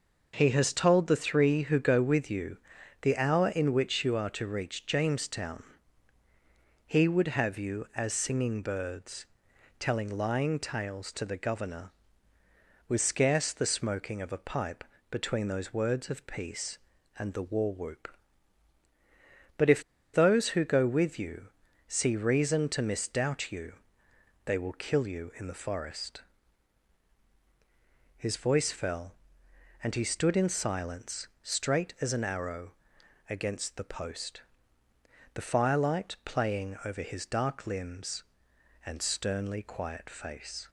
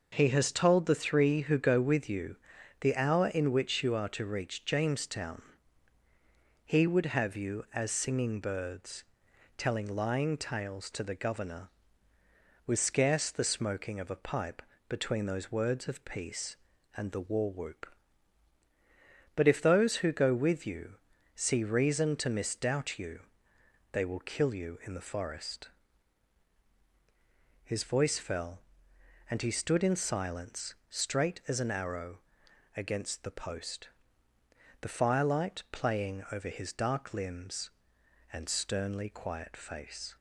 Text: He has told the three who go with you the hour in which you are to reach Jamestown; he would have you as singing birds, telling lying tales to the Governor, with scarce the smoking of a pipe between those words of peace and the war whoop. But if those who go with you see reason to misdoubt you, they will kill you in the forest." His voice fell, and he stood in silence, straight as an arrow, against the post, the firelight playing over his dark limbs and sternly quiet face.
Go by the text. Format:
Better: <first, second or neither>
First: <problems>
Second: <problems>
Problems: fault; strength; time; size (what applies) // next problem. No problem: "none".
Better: second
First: pauses between "you" and "the"; noticeable; at 2.5 s; 0.46 s long // pauses between "pipe" and "between"; slight; at 14.8 s; 0.26 s long // pauses between "if" and "those"; slight; at 19.8 s; 0.32 s long // pauses between "you" and "see"; at 21.4 s; 0.38 s long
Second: pauses between "you" and "the"; noticeable; at 2.3 s; 0.46 s long // pauses between "pipe" and "between"; slight; at 14.6 s; 0.26 s long // pauses between "you" and "see"; at 20.9 s; 0.38 s long